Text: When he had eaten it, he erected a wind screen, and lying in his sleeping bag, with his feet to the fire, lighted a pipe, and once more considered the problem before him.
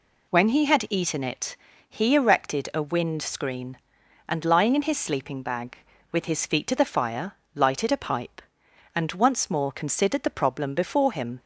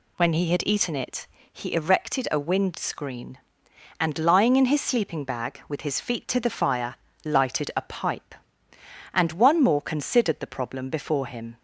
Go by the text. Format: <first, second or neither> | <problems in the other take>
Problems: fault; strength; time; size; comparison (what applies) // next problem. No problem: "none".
first | says "one" for "once"; at 9.3 s